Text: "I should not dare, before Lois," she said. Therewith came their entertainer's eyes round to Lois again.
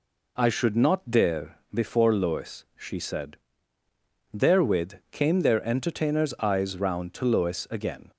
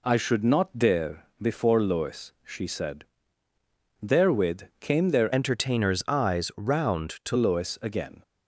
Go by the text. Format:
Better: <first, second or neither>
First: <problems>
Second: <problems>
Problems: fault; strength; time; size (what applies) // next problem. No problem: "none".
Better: first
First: pauses between "Therewith" and "came"; slight; at 4.9 s; 0.16 s long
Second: pauses between "Therewith" and "came"; slight; at 4.6 s; 0.16 s long // changes voice from "entertainer's" to "to"; from 5.3 to 7.3 s; 2.0 s long